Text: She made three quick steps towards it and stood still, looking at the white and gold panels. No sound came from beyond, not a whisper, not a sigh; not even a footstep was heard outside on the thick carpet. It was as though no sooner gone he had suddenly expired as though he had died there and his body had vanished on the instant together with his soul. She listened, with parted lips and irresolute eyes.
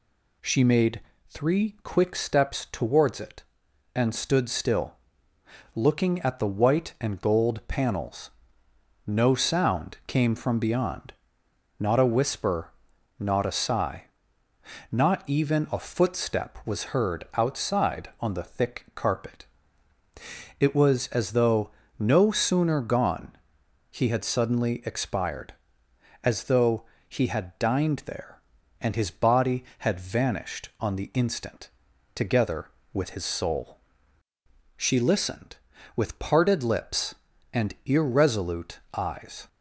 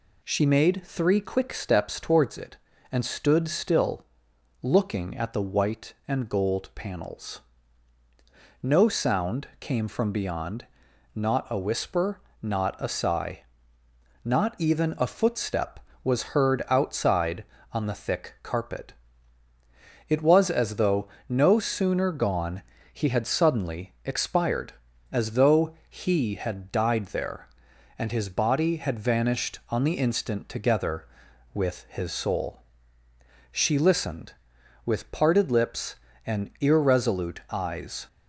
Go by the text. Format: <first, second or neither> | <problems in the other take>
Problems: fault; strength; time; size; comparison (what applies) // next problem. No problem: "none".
second | pauses between "made" and "three"; slight; at 0.9 s; 0.30 s long // pauses between "though" and "no"; slight; at 21.6 s; 0.28 s long; slight in the second // pauses between "gone" and "he"; noticeable; at 23.3 s; 0.58 s long; slight in the second // pauses between "though" and "he"; slight; at 26.8 s; 0.24 s long // says "dined" for "died"; at 27.5 s // pauses between "instant" and "together"; at 31.6 s; 0.44 s long // pauses between "irresolute" and "eyes"; slight; at 38.7 s; 0.16 s long